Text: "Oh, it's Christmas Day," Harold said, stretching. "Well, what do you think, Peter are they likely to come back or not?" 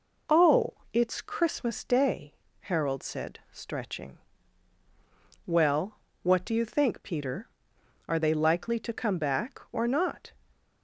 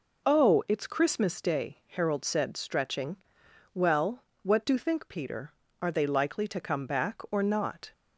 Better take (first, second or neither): first